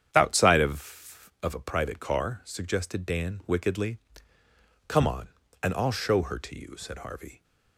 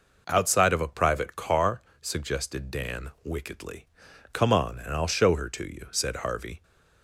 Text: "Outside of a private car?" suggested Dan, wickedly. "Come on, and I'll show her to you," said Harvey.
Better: second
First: starts louder than the rest; strong; until 1.1 s; 8.5 dB // says "of" twice; at 1.4 s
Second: none

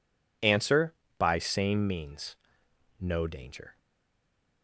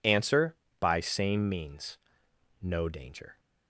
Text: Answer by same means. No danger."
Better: second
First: stays silent after the last word; slight; from 3.7 s on; 0.9 s long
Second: none

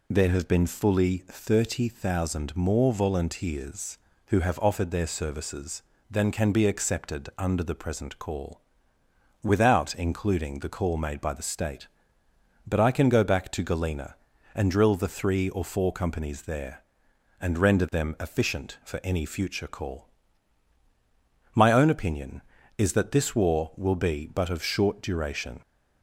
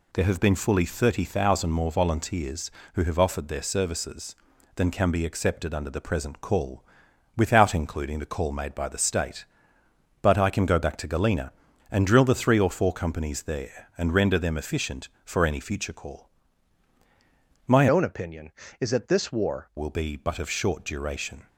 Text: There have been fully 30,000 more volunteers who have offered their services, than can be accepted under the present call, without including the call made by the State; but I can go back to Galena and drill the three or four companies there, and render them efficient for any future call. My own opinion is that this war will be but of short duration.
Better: first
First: none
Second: changes voice from "own" to "war"; from 17.8 to 19.6 s; 1.8 s long

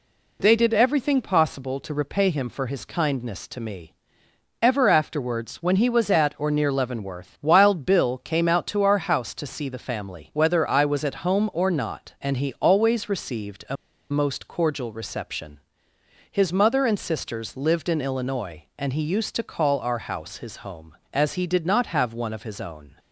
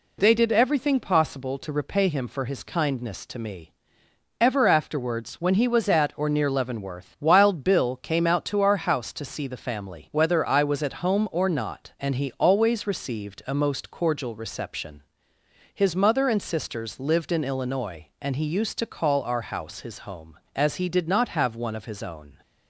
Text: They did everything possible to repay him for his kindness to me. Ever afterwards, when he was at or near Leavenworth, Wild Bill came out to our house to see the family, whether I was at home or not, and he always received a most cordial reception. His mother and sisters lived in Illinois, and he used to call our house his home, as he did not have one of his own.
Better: second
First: pauses between "a" and "most"; slight; at 13.7 s; 0.35 s long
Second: none

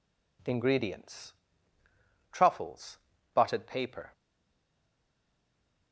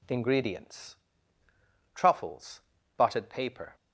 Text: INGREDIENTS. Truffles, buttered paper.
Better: second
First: stays silent after the last word; noticeable; from 4.1 s on; 1.8 s long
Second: none

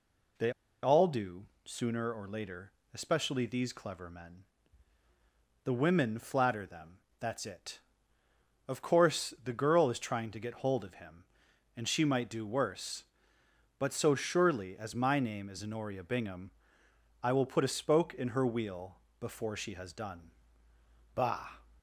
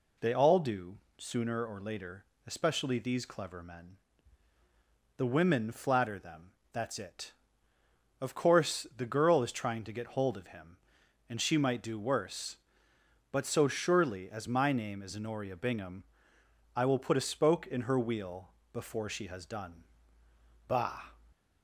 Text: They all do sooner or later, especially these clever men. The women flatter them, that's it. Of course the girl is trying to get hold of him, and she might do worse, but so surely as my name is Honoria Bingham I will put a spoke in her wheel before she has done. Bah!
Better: second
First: pauses between "They" and "all"; slight; at 0.5 s; 0.31 s long // pauses between "do" and "sooner"; slight; at 1.4 s; 0.20 s long // pauses between "Bingham" and "I"; noticeable; at 16.4 s; 0.72 s long // pauses between "wheel" and "before"; slight; at 18.9 s; 0.22 s long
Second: pauses between "do" and "sooner"; slight; at 0.9 s; 0.21 s long // pauses between "Bingham" and "I"; noticeable; at 16.0 s; 0.72 s long // pauses between "wheel" and "before"; slight; at 18.5 s; 0.22 s long

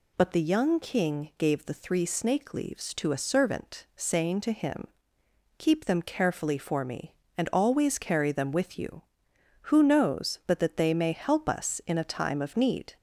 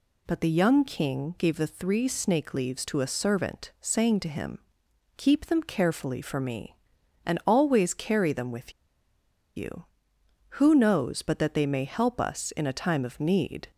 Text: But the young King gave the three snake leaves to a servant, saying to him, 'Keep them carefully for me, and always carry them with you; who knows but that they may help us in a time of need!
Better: first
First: none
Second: pauses between "with" and "you"; noticeable; at 8.7 s; 0.84 s long

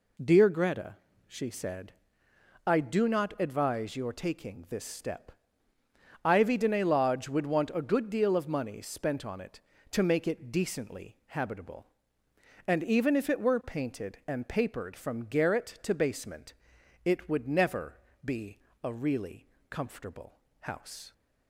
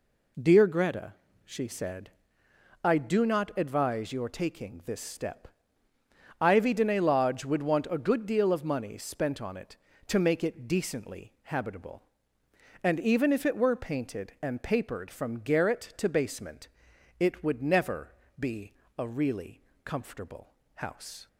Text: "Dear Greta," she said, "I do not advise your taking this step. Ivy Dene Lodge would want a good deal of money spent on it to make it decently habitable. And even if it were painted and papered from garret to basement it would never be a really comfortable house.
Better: neither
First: pauses between "basement" and "it"; noticeable; at 16.5 s; 0.50 s long // pauses between "never" and "be"; slight; at 17.9 s; 0.26 s long // pauses between "be" and "a"; slight; at 18.5 s; 0.26 s long // pauses between "really" and "comfortable"; slight; at 19.4 s; 0.22 s long // pauses between "comfortable" and "house"; slight; at 20.3 s; 0.22 s long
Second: pauses between "basement" and "it"; noticeable; at 16.6 s; 0.50 s long // pauses between "never" and "be"; slight; at 18.1 s; 0.26 s long // pauses between "be" and "a"; slight; at 18.7 s; 0.26 s long // pauses between "really" and "comfortable"; slight; at 19.6 s; 0.22 s long // pauses between "comfortable" and "house"; slight; at 20.5 s; 0.22 s long

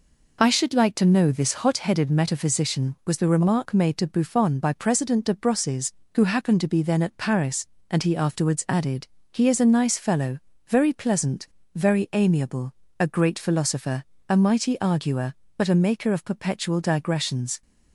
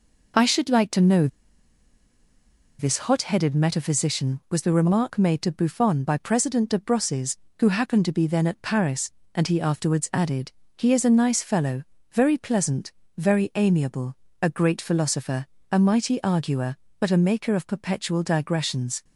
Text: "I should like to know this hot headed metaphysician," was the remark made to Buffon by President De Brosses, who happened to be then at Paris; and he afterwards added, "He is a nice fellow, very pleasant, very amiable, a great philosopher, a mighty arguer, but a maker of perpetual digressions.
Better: first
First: none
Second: pauses between "know" and "this"; strong; at 1.2 s; 1.5 s long

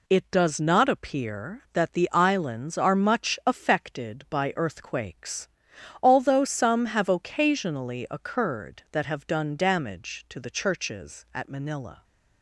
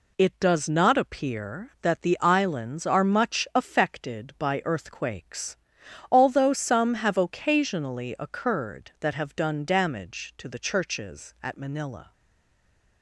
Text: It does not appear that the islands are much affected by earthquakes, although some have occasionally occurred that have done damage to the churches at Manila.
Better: first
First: none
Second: stays silent after the last word; slight; from 12.1 s on; 0.9 s long

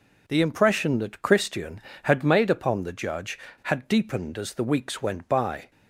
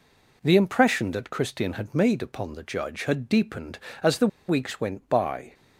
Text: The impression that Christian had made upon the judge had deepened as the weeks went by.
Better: first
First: none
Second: pauses between "the" and "weeks"; slight; at 4.2 s; 0.21 s long

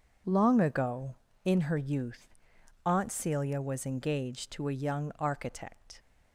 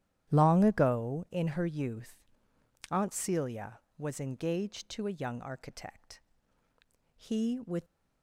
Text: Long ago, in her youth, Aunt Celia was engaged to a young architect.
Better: first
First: none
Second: starts louder than the rest; strong; until 1.3 s; 11.5 dB // goes on to say "He with"; noticeable; from 7.1 s on; 0.68 s long

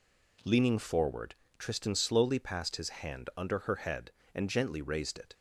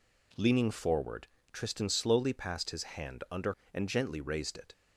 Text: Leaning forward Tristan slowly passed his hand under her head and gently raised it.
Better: first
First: pauses between "forward" and "Tristan"; slight; at 1.3 s; 0.22 s long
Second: pauses between "forward" and "Tristan"; slight; at 1.2 s; 0.24 s long // skips "her head"; at 3.6 s

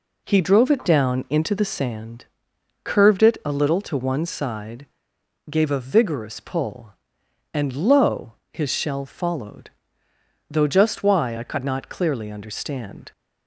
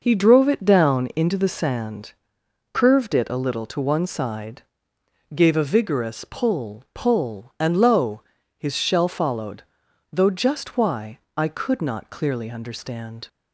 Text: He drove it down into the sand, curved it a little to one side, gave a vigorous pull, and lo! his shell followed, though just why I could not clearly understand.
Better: first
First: none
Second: says "pull" twice; at 6.9 s // pauses between "why" and "I"; slight; at 11.1 s; 0.18 s long

